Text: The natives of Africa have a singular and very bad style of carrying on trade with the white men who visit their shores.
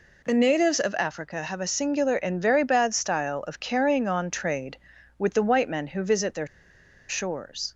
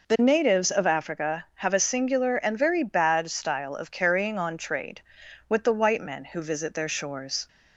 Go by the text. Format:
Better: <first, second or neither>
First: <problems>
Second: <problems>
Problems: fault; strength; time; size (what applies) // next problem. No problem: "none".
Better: second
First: pauses between "their" and "shores"; noticeable; at 6.4 s; 0.62 s long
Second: none